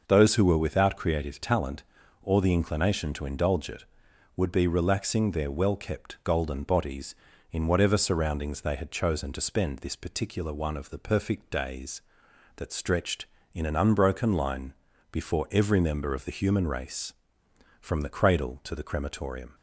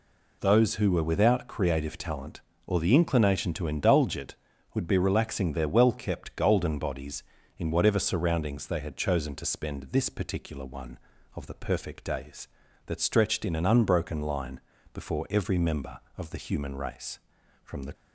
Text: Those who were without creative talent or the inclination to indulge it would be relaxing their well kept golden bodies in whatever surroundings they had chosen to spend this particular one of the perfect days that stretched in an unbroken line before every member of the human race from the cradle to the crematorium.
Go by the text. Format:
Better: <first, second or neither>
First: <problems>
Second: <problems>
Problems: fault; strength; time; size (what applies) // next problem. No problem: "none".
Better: first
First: pauses between "line" and "before"; at 14.7 s; 0.38 s long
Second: pauses between "line" and "before"; slight; at 14.5 s; 0.34 s long // stops before "cradle to the crematorium"; at 17.9 s